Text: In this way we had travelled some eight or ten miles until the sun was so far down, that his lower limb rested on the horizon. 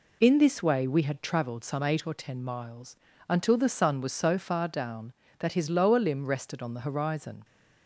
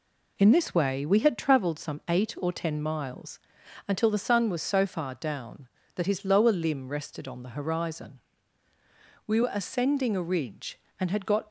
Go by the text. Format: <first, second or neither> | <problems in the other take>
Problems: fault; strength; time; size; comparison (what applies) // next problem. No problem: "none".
first | pauses between "miles" and "until"; noticeable; at 3.3 s; 0.50 s long; slight in the first // goes on to say "We were ascending a ridge and had got"; strong; from 9.2 s on; 2.2 s long